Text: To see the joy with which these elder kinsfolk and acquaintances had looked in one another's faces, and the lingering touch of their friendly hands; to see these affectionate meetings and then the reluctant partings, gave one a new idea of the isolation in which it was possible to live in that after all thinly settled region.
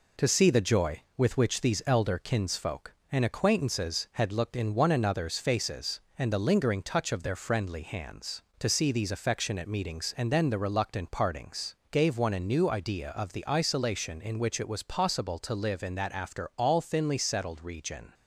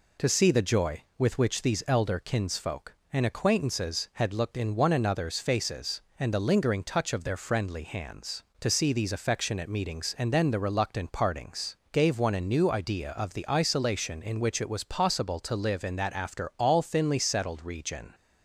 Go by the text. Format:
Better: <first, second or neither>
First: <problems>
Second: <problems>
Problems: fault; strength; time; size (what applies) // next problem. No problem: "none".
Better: second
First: gets quieter; throughout; 3.5 dB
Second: none